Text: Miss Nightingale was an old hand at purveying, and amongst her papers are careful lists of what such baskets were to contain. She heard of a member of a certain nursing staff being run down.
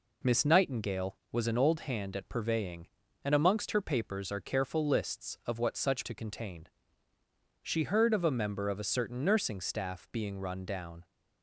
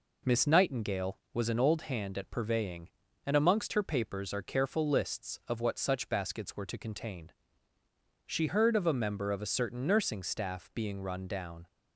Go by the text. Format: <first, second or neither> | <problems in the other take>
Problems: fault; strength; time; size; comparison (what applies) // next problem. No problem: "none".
second | skips "baskets were"; at 6.0 s